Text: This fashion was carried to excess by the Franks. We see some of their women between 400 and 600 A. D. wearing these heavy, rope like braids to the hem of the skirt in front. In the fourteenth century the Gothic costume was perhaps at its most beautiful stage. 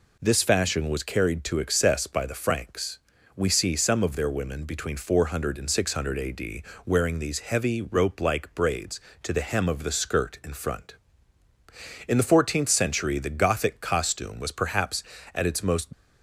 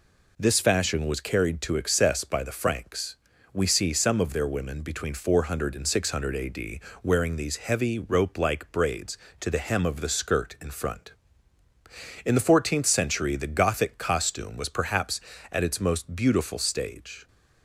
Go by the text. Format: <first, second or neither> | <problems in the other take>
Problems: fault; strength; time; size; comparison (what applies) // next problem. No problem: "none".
second | pauses between "D" and "wearing"; slight; at 6.6 s; 0.22 s long; slight in the second // stops before "beautiful stage"; at 15.9 s